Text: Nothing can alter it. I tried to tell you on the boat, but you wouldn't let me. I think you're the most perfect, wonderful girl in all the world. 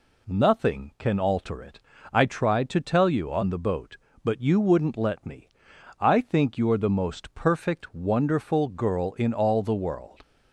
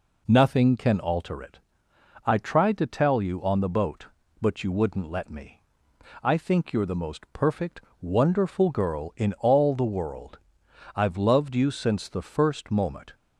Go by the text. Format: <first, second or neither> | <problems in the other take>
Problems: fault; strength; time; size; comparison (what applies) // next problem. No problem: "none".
first | goes on to say "I've loved you since the first moment"; strong; from 10.9 s on; 2.1 s long